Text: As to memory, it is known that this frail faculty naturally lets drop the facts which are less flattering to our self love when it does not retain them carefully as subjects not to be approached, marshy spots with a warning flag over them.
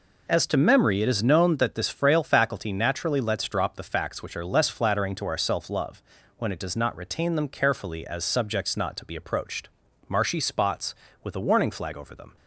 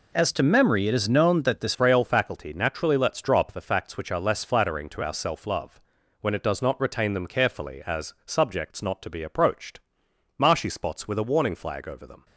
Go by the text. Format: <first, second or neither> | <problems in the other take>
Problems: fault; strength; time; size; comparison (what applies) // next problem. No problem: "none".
first | changes voice at "frail"; from 1.7 s on; 10.5 s long // pauses between "love" and "when"; at 5.8 s; 0.40 s long; slight in the first